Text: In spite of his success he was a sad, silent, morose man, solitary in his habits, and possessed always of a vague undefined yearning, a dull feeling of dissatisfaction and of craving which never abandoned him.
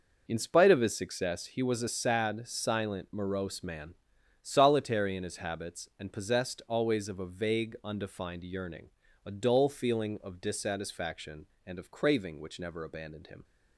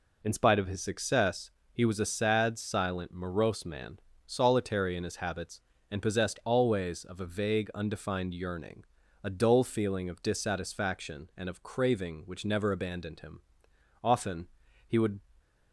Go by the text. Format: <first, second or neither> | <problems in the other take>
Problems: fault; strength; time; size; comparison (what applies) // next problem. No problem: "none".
first | pauses between "success" and "he"; slight; at 1.4 s; 0.24 s long // goes on to say "Often he would"; noticeable; from 14.0 s on; 1.1 s long